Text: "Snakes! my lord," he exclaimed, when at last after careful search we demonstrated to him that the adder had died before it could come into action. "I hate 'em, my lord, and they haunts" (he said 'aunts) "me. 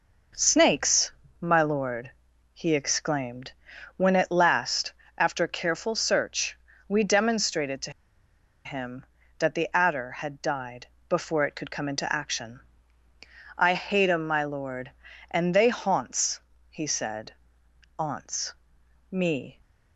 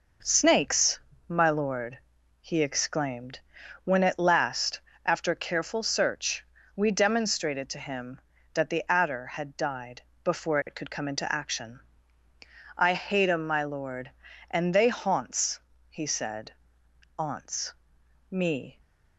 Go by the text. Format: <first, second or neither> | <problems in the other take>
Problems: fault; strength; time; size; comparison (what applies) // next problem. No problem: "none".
second | pauses between "last" and "after"; slight; at 4.9 s; 0.24 s long; slight in the second // pauses between "search" and "we"; slight; at 6.5 s; 0.30 s long; slight in the second // pauses between "to" and "him"; noticeable; at 7.9 s; 0.73 s long // pauses between "died" and "before"; slight; at 10.8 s; 0.24 s long; slight in the second // pauses between "said" and "aunts"; noticeable; at 17.3 s; 0.64 s long; noticeable in the second